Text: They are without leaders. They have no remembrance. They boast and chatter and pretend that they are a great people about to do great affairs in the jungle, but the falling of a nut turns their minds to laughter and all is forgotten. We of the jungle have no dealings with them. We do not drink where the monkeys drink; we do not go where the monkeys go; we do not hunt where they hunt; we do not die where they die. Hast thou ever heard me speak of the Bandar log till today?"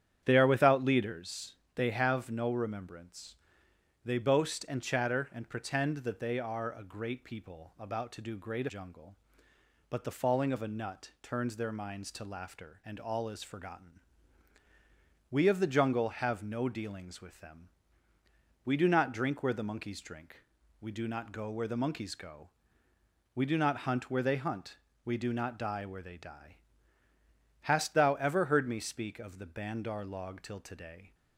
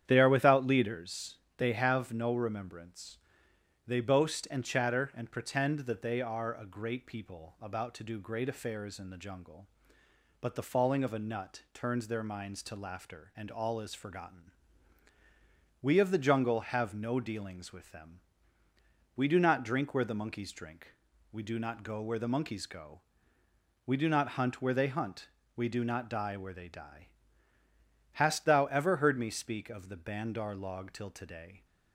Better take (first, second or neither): second